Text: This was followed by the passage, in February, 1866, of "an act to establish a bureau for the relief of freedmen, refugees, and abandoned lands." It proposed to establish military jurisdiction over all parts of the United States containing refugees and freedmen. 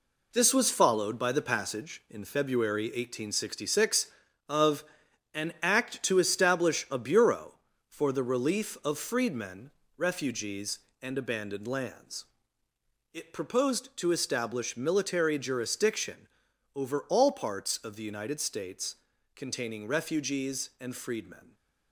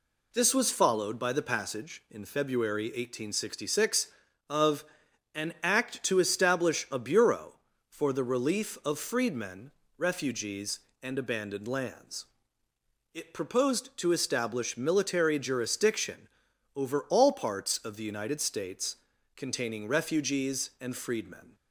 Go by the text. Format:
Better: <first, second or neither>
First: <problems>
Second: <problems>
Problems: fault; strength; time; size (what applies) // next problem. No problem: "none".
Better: second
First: gets quieter; strong; throughout; 7.5 dB // pauses between "of" and "an"; noticeable; at 4.8 s; 0.50 s long // pauses between "jurisdiction" and "over"; noticeable; at 16.2 s; 0.48 s long // pauses between "States" and "containing"; at 18.9 s; 0.38 s long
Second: pauses between "of" and "an"; noticeable; at 4.8 s; 0.50 s long // pauses between "jurisdiction" and "over"; noticeable; at 16.2 s; 0.48 s long // pauses between "States" and "containing"; at 18.9 s; 0.38 s long